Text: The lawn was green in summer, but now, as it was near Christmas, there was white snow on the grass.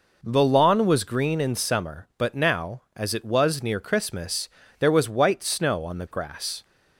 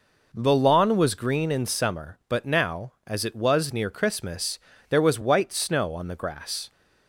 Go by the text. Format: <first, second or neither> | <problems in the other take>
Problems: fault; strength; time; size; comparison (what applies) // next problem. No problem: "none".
neither | none